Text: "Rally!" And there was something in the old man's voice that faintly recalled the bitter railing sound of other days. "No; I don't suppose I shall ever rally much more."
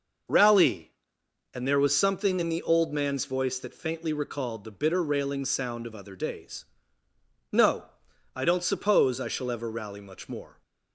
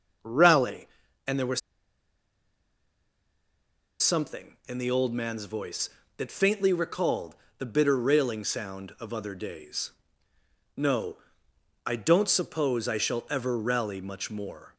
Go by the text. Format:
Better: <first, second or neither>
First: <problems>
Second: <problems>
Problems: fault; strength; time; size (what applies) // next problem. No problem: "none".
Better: first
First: none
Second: starts louder than the rest; noticeable; until 4.0 s; 6 dB // pauses between "was" and "something"; strong; at 1.6 s; 2.4 s long // pauses between "recalled" and "the"; slight; at 7.3 s; 0.24 s long